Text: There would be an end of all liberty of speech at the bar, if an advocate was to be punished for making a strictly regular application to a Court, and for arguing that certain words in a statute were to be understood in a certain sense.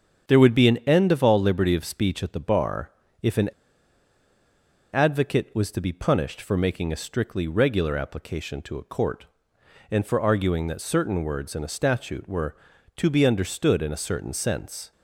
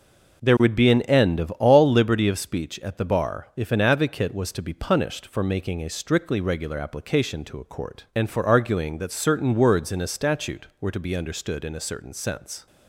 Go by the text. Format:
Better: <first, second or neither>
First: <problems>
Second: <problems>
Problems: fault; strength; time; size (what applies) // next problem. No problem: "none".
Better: second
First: starts louder than the rest; until 1.2 s; 7 dB // pauses between "an" and "advocate"; strong; at 3.4 s; 1.4 s long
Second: none